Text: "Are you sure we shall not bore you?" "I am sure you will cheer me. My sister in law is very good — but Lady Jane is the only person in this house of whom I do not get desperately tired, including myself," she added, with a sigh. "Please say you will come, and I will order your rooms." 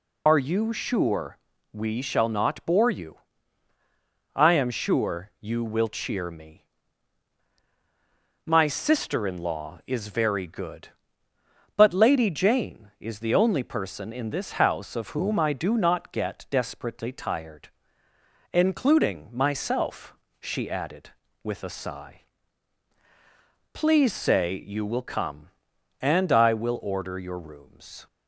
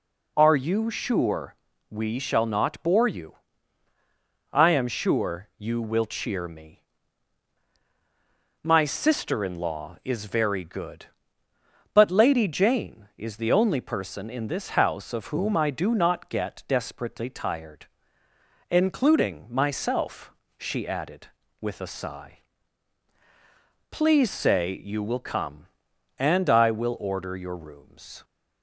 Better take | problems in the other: second | loses the start of "Are"; at 0.2 s; 75 ms // pauses between "sure" and "we"; slight; at 1.3 s; 0.36 s long; slight in the second

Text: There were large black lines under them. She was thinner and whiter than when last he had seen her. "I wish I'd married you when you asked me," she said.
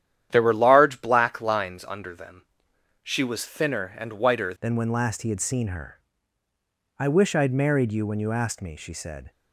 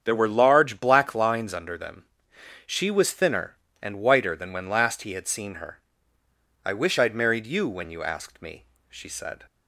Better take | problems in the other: second | starts louder than the rest; strong; until 1.3 s; 10.5 dB; strong in the second // changes voice at "than"; from 4.6 s on; 4.7 s long

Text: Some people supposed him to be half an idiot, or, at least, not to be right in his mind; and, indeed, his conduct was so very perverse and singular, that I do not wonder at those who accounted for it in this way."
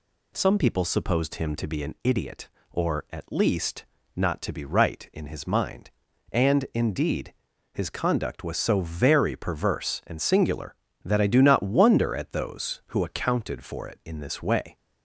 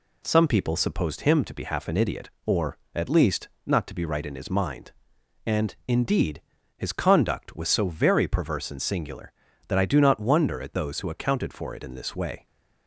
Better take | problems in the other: second | skips "half"; at 1.8 s

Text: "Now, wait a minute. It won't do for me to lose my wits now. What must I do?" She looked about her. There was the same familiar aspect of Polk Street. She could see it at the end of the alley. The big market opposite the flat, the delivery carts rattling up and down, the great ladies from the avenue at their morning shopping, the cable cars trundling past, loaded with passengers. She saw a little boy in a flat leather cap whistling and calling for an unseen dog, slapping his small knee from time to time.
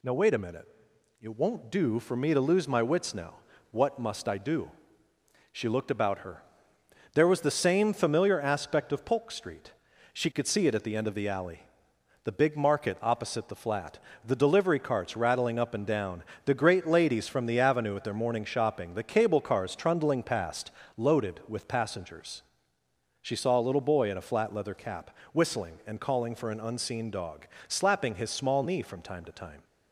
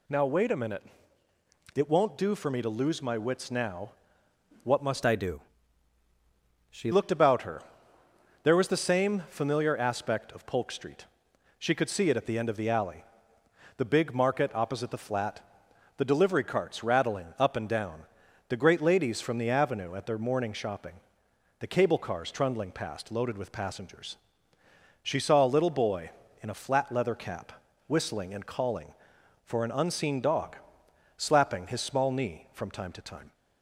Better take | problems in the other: first | changes voice from "I" to "She"; from 5.0 to 6.9 s; 1.9 s long // pauses between "cap" and "whistling"; slight; at 27.5 s; 0.34 s long; slight in the first

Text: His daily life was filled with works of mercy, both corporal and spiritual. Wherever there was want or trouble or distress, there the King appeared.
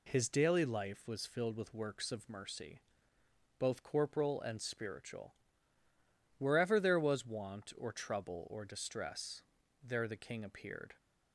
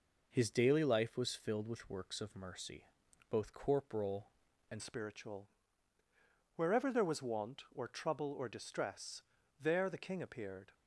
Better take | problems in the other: first | changes voice at "spiritual"; from 4.7 s on; 6.0 s long

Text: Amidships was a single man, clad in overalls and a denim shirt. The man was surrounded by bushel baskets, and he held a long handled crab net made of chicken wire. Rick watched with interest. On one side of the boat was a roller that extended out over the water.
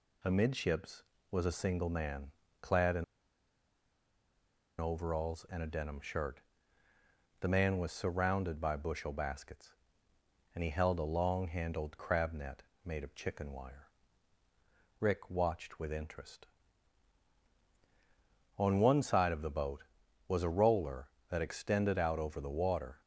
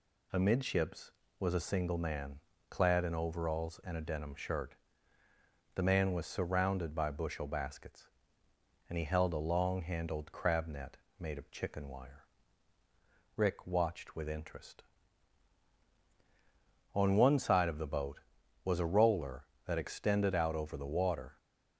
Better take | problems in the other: second | pauses between "in" and "overalls"; strong; at 3.0 s; 1.7 s long // pauses between "net" and "made"; slight; at 12.6 s; 0.20 s long; slight in the second

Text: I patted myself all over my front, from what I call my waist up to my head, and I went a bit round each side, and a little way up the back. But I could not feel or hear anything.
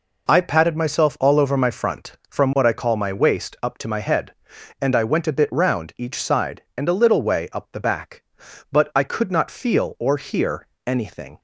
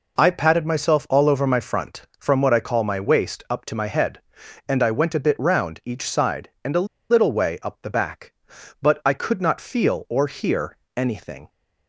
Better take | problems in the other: first | pauses between "a" and "little"; slight; at 6.8 s; 0.23 s long // pauses between "hear" and "anything"; slight; at 10.7 s; 0.18 s long; slight in the first

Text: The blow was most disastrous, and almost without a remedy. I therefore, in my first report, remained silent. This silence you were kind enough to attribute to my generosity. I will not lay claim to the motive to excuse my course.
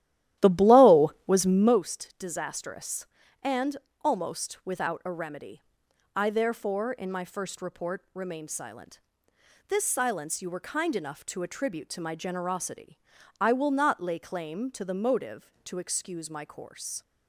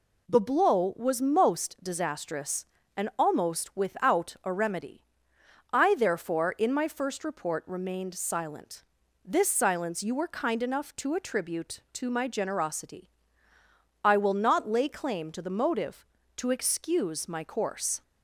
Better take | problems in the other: second | starts louder than the rest; strong; until 1.8 s; 13 dB // pauses between "and" and "almost"; slight; at 3.7 s; 0.28 s long

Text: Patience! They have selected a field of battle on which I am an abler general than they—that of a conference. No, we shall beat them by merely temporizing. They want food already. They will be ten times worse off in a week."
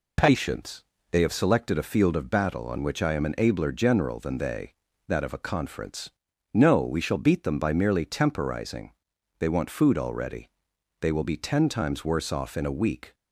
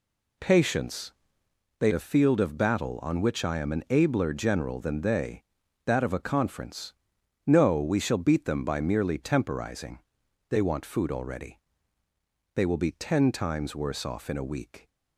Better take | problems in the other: first | skips "have selected"; at 1.9 s

